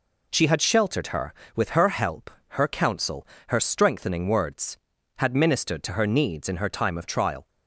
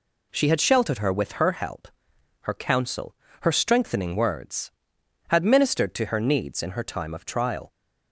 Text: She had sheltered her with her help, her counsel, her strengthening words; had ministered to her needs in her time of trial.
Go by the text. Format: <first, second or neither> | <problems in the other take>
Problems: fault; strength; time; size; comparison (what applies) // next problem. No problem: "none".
neither | none